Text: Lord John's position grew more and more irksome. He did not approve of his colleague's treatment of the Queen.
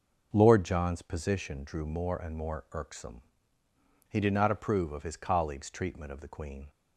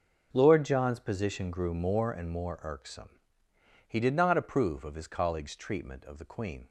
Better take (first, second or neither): second